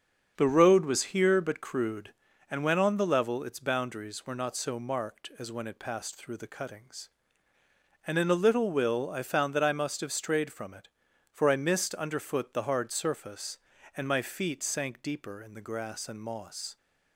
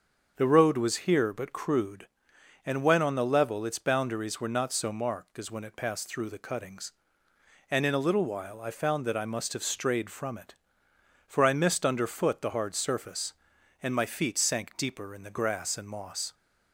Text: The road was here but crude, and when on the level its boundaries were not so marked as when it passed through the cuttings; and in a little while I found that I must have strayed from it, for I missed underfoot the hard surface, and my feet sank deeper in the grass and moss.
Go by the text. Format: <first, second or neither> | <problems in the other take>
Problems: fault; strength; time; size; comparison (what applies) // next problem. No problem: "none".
second | starts louder than the rest; strong; until 1.3 s; 7 dB; also in the second // says "will" for "while"; at 8.7 s